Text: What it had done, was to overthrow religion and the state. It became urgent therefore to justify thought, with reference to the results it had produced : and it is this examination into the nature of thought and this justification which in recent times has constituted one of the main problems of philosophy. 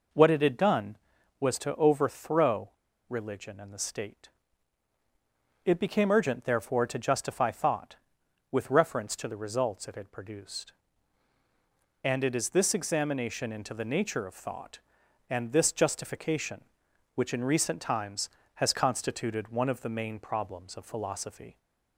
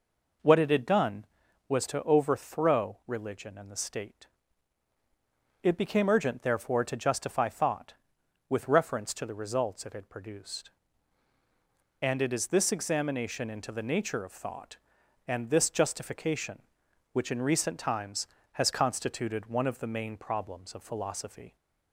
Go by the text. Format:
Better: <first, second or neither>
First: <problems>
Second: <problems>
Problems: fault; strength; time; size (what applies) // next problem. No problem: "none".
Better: second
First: pauses between "overthrow" and "religion"; at 2.6 s; 0.40 s long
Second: none